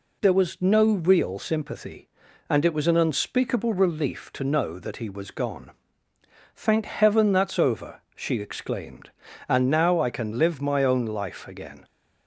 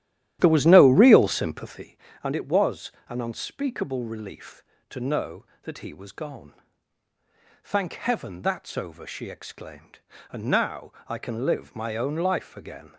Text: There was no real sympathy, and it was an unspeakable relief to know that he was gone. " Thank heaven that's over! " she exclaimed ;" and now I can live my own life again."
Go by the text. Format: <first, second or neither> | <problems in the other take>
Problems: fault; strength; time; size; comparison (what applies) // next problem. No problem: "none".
first | starts louder than the rest; strong; until 2.0 s; 14 dB // pauses between "was" and "an"; slight; at 2.9 s; 0.18 s long